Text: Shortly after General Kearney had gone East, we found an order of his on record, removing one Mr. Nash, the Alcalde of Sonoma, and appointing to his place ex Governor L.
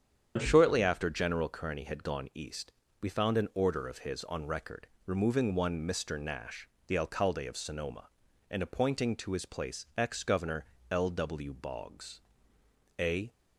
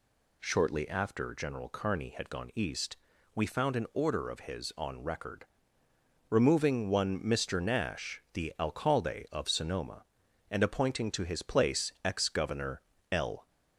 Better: second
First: starts louder than the rest; strong; until 1.3 s; 8.5 dB // pauses between "Governor" and "L"; slight; at 10.6 s; 0.26 s long // goes on to say "W Boggs A"; strong; from 11.0 s on; 2.2 s long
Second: pauses between "Governor" and "L"; slight; at 12.8 s; 0.30 s long

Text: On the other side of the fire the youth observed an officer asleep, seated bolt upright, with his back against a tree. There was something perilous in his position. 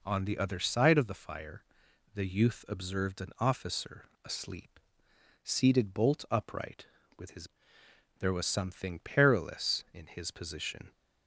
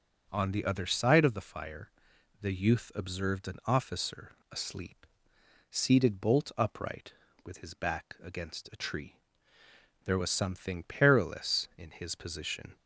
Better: second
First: pauses between "fire" and "the"; noticeable; at 1.6 s; 0.52 s long // pauses between "officer" and "asleep"; slight; at 4.0 s; 0.18 s long // skips "back against a tree"; at 7.8 s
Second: pauses between "fire" and "the"; noticeable; at 1.8 s; 0.52 s long // pauses between "officer" and "asleep"; slight; at 4.3 s; 0.18 s long

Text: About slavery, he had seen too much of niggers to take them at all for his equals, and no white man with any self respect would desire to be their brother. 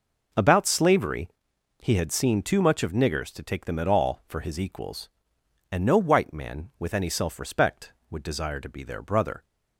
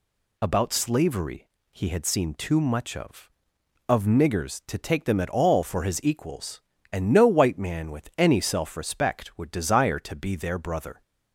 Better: first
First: none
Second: says "of" twice; at 3.8 s

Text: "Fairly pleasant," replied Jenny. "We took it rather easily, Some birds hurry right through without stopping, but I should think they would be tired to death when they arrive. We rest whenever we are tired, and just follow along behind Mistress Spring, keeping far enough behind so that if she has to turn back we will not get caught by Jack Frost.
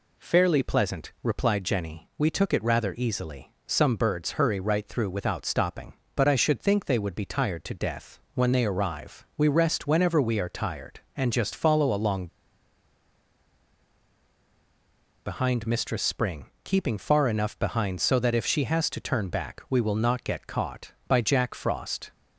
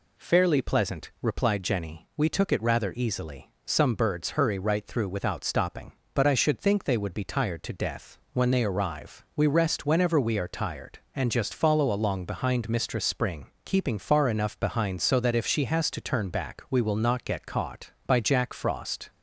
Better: second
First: pauses between "death" and "when"; slight; at 8.1 s; 0.16 s long // pauses between "along" and "behind"; strong; at 12.2 s; 2.9 s long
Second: pauses between "death" and "when"; slight; at 8.1 s; 0.16 s long

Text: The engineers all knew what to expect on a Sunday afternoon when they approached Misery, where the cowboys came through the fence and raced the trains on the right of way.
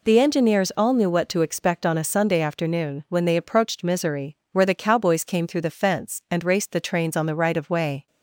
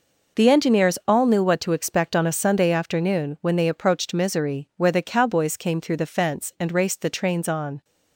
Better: first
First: none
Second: stops before "the right of way"; at 7.8 s

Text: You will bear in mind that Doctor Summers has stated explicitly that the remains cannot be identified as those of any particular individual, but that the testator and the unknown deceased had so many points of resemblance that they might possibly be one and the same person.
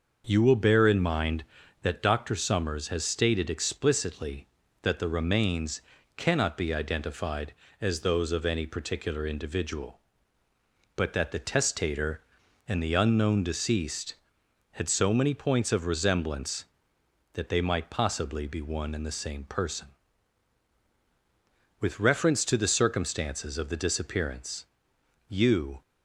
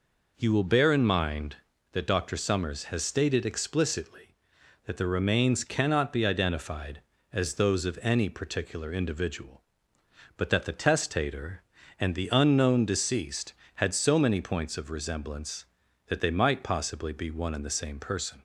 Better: second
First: pauses between "remains" and "cannot"; slight; at 5.8 s; 0.36 s long // goes on to say "With reference to the circumstances of the disappearance you"; strong; from 21.7 s on; 4.0 s long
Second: none

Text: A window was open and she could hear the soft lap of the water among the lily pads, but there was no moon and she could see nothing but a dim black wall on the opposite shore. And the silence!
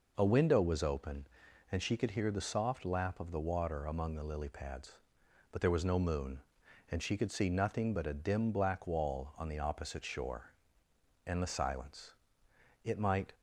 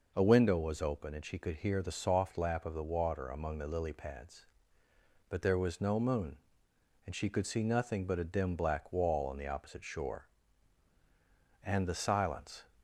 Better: second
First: goes on to say "It might"; slight; from 12.8 s on; 0.48 s long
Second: none

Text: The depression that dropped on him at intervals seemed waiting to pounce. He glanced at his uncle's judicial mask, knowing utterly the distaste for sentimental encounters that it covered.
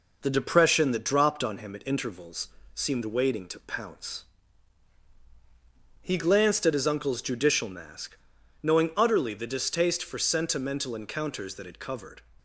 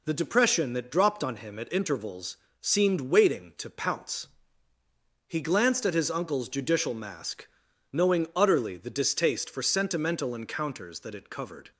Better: neither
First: pauses between "intervals" and "seemed"; slight; at 2.4 s; 0.26 s long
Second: pauses between "intervals" and "seemed"; slight; at 2.3 s; 0.24 s long

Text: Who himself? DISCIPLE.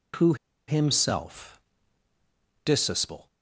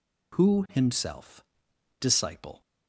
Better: second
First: pauses between "Who" and "himself"; slight; at 0.3 s; 0.33 s long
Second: none

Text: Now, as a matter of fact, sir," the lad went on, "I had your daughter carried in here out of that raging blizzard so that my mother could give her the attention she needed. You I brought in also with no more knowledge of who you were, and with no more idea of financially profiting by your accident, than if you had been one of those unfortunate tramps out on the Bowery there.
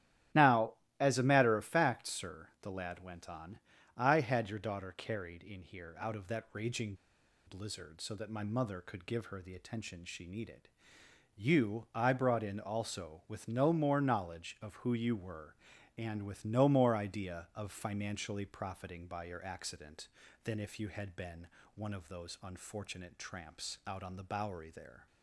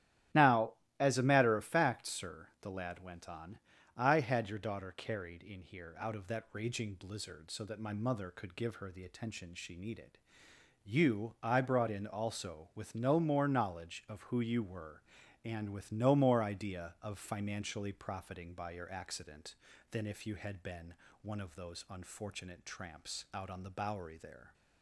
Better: second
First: starts louder than the rest; strong; until 1.5 s; 11.5 dB // pauses between "raging" and "blizzard"; noticeable; at 6.9 s; 0.52 s long // pauses between "been" and "one"; slight; at 21.4 s; 0.26 s long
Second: starts louder than the rest; strong; until 1.6 s; 12.5 dB // pauses between "been" and "one"; slight; at 20.9 s; 0.26 s long

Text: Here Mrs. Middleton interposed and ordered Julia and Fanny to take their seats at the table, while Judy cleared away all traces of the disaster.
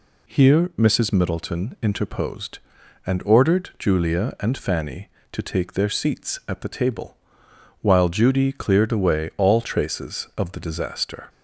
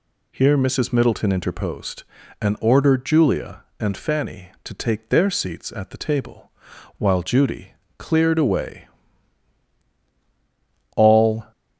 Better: first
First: none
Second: pauses between "Judy" and "cleared"; slight; at 7.7 s; 0.24 s long // pauses between "away" and "all"; strong; at 8.8 s; 2.0 s long // stops before "traces of the disaster"; at 11.5 s

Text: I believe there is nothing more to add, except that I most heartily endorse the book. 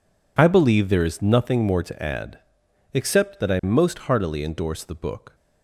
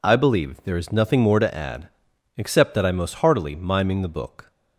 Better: first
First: none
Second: says "miming" for "endorse"; at 3.5 s

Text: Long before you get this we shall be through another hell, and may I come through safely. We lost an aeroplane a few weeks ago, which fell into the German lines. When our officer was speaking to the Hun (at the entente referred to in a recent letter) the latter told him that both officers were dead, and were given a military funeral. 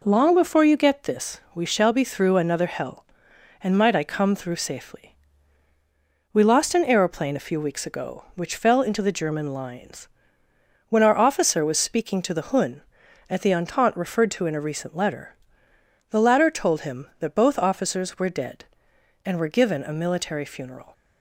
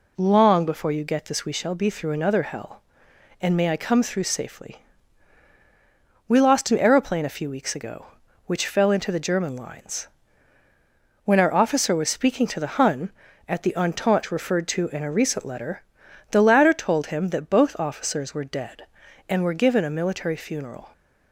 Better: second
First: pauses between "this" and "we"; slight; at 1.3 s; 0.16 s long // says "might" for "may"; at 3.7 s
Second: none

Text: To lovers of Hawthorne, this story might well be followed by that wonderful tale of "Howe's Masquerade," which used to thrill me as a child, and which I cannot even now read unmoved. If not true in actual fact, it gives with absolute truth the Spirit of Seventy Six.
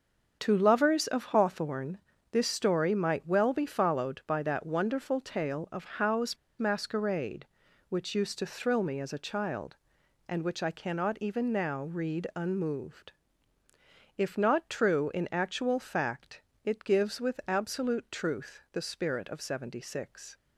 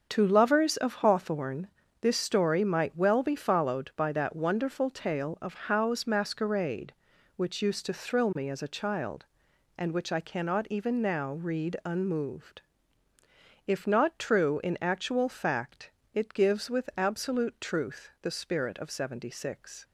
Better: second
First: starts louder than the rest; until 1.4 s; 6.5 dB // pauses between "Howe's" and "Masquerade"; slight; at 6.3 s; 0.22 s long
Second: starts louder than the rest; until 1.1 s; 6.5 dB

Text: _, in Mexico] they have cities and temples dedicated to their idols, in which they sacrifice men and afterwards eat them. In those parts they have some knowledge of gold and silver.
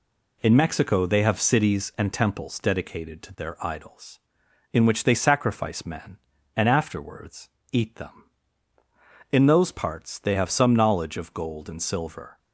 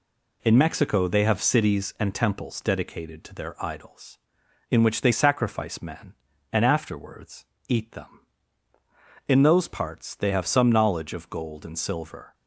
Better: neither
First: pauses between "afterwards" and "eat"; slight; at 7.4 s; 0.22 s long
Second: pauses between "afterwards" and "eat"; slight; at 7.4 s; 0.22 s long

